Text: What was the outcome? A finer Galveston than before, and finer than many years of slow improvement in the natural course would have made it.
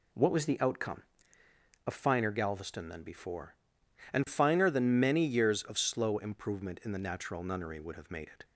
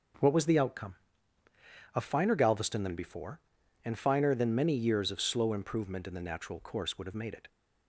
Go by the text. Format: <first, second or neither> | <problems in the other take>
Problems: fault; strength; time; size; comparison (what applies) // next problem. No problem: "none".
second | says "nunnery" for "course"; at 7.4 s